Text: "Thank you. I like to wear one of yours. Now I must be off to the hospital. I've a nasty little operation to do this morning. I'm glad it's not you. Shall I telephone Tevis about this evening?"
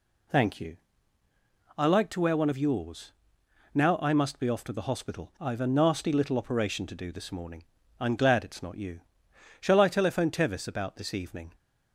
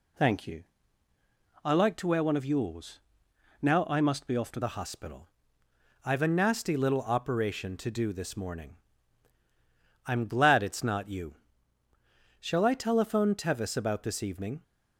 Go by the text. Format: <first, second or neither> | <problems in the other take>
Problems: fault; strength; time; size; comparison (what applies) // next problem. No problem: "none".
first | changes voice at "the"; from 4.6 s on; 10.0 s long